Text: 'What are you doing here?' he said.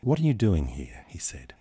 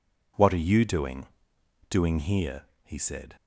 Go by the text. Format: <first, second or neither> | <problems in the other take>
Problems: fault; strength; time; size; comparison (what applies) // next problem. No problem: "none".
first | says "doing" twice; at 1.8 s